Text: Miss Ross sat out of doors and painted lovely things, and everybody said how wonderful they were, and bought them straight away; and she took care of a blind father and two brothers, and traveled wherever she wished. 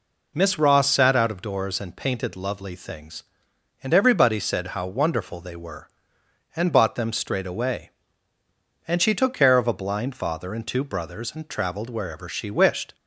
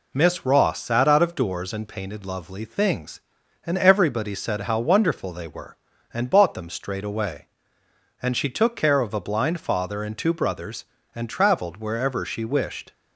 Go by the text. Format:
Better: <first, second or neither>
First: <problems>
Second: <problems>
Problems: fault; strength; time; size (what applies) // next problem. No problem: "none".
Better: neither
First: none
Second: none